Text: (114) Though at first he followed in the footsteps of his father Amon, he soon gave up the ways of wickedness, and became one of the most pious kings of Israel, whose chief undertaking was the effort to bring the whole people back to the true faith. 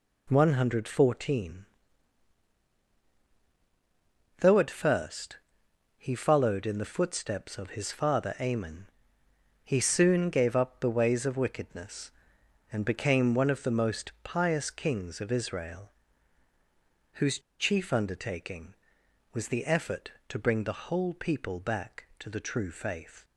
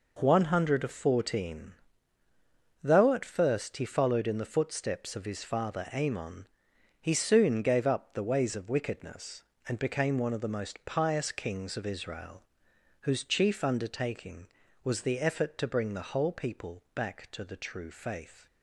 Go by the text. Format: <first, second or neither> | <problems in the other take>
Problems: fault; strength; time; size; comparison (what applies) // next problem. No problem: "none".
second | pauses between "first" and "he"; noticeable; at 5.3 s; 0.58 s long // pauses between "whose" and "chief"; slight; at 17.3 s; 0.20 s long